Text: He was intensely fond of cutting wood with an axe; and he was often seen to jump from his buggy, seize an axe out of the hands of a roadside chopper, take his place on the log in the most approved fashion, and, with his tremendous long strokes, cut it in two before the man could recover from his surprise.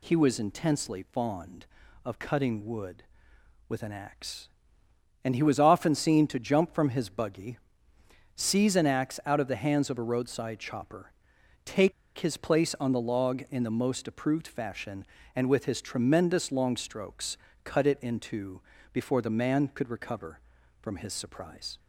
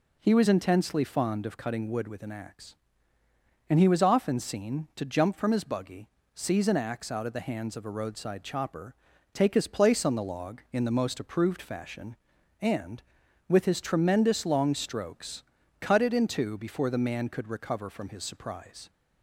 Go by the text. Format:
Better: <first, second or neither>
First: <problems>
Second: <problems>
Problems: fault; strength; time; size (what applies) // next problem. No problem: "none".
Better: second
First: pauses between "take" and "his"; slight; at 11.9 s; 0.25 s long // pauses between "two" and "before"; slight; at 18.6 s; 0.32 s long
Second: none